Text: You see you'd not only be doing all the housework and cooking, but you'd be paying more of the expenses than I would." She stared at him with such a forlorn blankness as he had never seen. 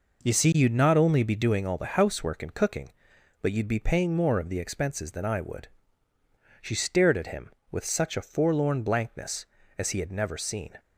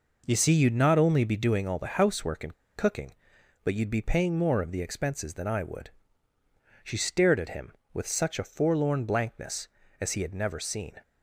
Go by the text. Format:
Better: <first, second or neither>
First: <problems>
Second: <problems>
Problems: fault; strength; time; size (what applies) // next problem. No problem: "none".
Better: first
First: none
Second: pauses between "and" and "cooking"; slight; at 2.5 s; 0.21 s long